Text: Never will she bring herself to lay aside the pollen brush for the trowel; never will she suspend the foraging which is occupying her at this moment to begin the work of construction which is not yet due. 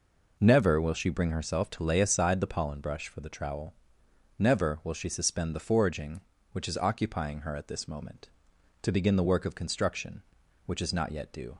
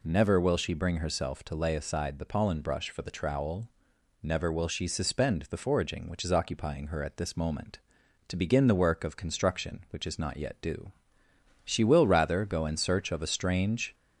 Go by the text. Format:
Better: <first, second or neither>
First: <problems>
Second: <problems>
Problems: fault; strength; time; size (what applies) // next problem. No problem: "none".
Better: first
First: none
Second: goes on to say "She will rather go in search of a strange"; strong; from 11.6 s on; 2.2 s long